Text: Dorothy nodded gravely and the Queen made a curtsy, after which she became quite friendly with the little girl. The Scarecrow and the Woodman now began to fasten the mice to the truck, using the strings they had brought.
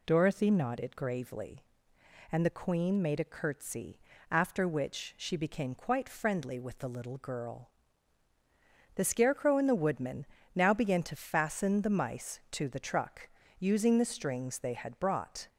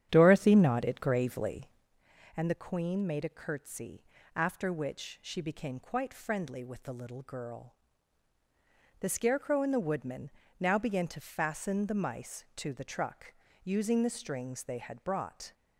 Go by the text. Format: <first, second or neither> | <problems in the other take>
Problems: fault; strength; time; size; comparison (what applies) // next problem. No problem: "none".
first | starts louder than the rest; strong; until 1.9 s; 9.5 dB // pauses between "Woodman" and "now"; slight; at 10.2 s; 0.30 s long; slight in the first